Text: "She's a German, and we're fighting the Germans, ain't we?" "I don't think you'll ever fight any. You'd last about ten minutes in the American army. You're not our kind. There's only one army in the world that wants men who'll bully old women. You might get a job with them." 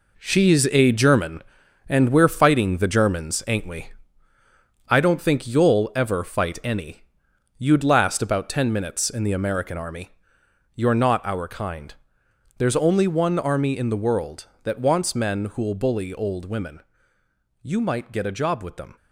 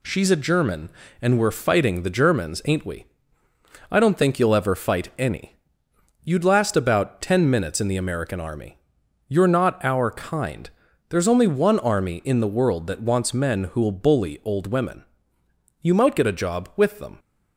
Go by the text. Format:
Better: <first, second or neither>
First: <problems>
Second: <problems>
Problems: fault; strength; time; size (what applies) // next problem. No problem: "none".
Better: second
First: gets quieter; strong; throughout; 8.5 dB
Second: none